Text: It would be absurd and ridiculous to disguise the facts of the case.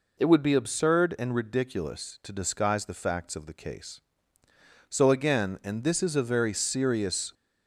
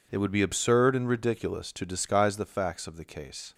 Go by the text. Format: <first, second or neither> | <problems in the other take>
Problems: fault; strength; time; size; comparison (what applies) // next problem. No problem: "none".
second | goes on to say "So again and this is a very serious"; strong; from 4.8 s on; 2.4 s long